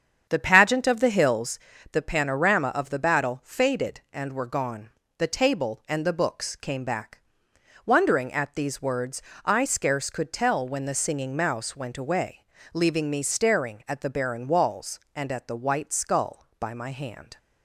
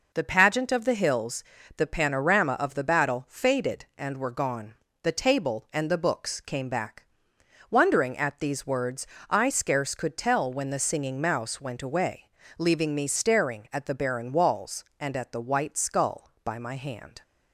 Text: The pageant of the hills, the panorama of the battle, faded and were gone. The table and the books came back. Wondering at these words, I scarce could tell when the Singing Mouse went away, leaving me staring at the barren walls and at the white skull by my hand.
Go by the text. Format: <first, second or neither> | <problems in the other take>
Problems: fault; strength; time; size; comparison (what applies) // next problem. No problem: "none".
second | starts louder than the rest; strong; until 1.7 s; 8 dB